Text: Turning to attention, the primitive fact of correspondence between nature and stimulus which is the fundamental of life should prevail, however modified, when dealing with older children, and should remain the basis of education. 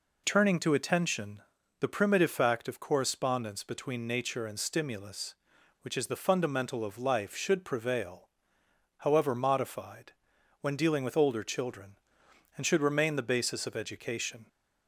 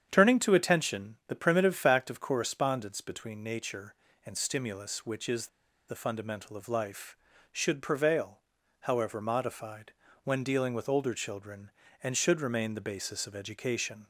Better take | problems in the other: first | starts louder than the rest; strong; until 1.1 s; 8.5 dB // pauses between "is" and "the"; at 5.4 s; 0.41 s long

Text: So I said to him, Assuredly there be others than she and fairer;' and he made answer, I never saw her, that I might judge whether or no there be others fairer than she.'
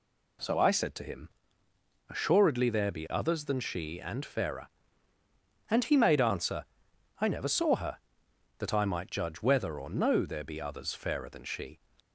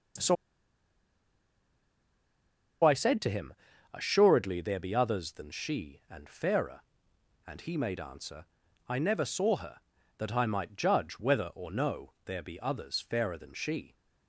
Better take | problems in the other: first | pauses between "So" and "I"; strong; at 0.3 s; 2.4 s long

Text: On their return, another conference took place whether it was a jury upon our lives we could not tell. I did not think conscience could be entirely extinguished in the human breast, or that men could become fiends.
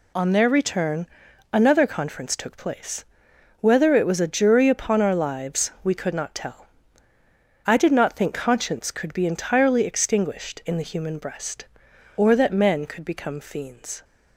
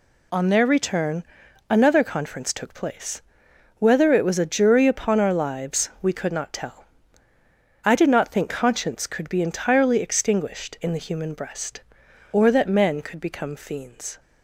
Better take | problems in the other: neither | pauses between "place" and "whether"; noticeable; the same in both

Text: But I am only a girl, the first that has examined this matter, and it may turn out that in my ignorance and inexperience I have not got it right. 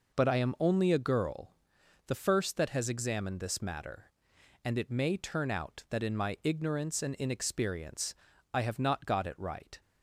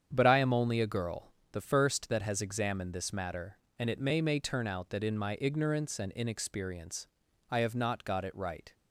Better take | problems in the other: first | starts louder than the rest; strong; until 1.1 s; 8 dB // says "may" twice; at 4.1 s // pauses between "inexperience" and "I"; at 7.0 s; 0.42 s long; also in the first

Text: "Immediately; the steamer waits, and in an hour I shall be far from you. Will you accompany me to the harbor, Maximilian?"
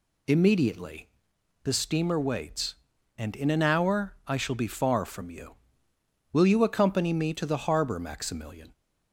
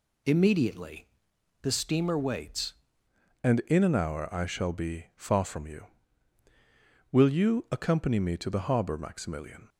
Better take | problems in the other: first | changes voice at "and"; from 3.4 s on; 6.2 s long

